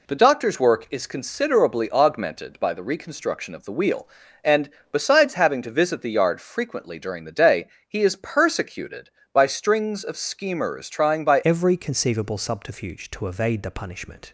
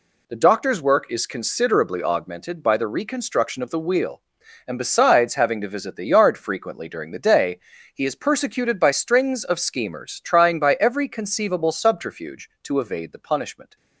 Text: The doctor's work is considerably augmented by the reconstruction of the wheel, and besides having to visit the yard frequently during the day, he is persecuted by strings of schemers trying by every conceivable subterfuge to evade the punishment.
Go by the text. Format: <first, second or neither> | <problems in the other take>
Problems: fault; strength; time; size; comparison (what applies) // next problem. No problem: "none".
second | pauses between "and" and "besides"; slight; at 4.6 s; 0.22 s long // changes voice at "every"; from 11.4 s on; 2.9 s long